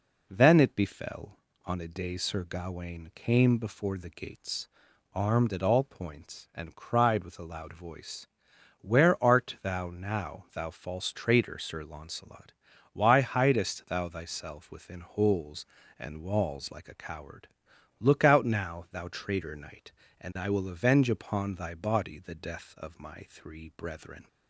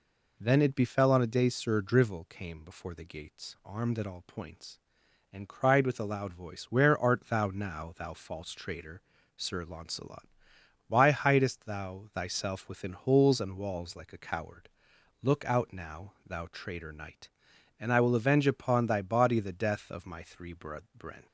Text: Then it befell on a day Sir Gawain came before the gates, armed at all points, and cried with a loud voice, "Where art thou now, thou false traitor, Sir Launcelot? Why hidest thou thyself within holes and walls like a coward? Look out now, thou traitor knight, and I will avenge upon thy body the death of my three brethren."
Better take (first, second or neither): first